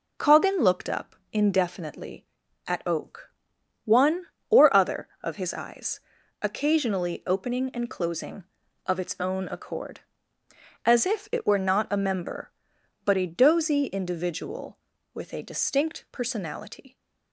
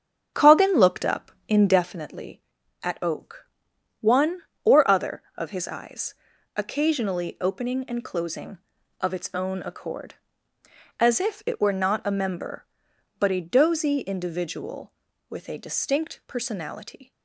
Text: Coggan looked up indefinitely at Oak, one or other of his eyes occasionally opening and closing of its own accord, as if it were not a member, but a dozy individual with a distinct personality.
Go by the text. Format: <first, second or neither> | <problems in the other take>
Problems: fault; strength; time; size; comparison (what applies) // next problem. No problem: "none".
first | starts louder than the rest; strong; until 1.9 s; 8 dB // pauses between "up" and "indefinitely"; slight; at 1.3 s; 0.16 s long; slight in the first // pauses between "eyes" and "occasionally"; at 6.1 s; 0.40 s long; also in the first